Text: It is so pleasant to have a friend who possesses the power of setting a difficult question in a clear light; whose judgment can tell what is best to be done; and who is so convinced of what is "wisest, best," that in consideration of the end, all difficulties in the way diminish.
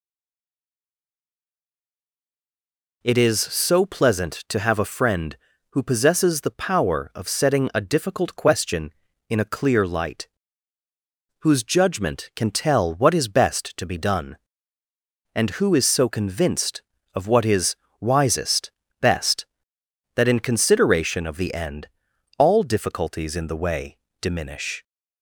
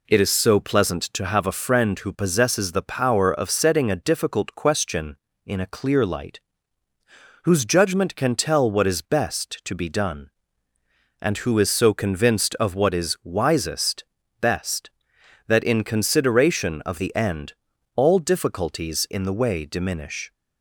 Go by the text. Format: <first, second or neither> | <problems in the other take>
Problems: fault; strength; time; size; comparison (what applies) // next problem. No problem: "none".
second | stays silent before the first word; strong; until 3.0 s; 3.0 s long // pauses between "is" and "wisest"; slight; at 17.7 s; 0.26 s long // pauses between "way" and "diminish"; slight; at 23.9 s; 0.22 s long